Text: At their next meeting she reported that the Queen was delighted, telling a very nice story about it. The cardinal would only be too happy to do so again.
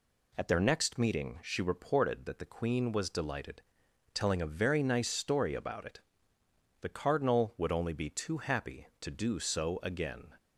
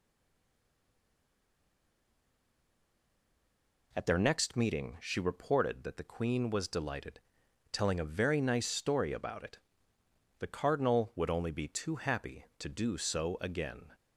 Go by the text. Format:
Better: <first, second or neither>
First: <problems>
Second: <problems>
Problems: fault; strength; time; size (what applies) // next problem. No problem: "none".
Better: first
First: none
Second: stays silent before the first word; strong; until 3.9 s; 3.9 s long